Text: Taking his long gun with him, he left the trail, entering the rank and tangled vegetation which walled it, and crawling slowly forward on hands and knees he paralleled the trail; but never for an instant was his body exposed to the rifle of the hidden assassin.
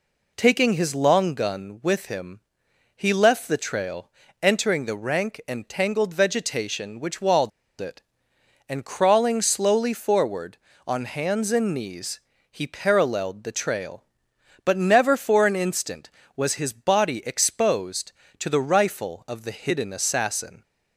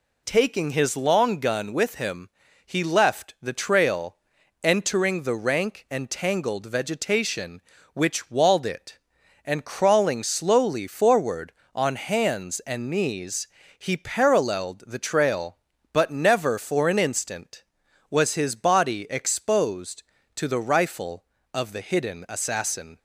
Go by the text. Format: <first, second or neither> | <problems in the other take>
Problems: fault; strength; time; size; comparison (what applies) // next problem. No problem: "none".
second | pauses between "walled" and "it"; slight; at 7.5 s; 0.31 s long // pauses between "knees" and "he"; slight; at 12.1 s; 0.32 s long; slight in the second